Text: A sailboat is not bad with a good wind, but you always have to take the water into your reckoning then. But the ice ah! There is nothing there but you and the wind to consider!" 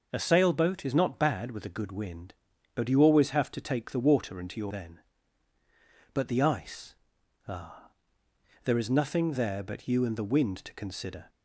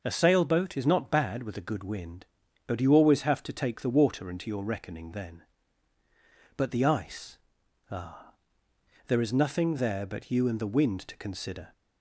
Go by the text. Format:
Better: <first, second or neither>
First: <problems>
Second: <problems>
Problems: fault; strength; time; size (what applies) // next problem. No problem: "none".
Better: second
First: skips "reckoning"; at 4.7 s // pauses between "ice" and "ah"; noticeable; at 6.9 s; 0.52 s long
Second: pauses between "ice" and "ah"; noticeable; at 7.3 s; 0.52 s long